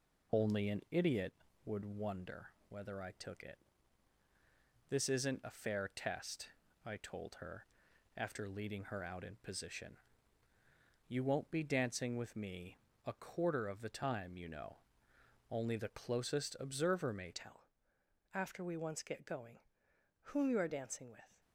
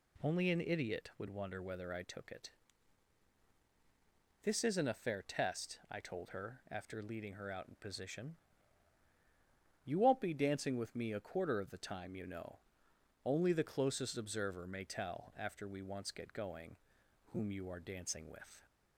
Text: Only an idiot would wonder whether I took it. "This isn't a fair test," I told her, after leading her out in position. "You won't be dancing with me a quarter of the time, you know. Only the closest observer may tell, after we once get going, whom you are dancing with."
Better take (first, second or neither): second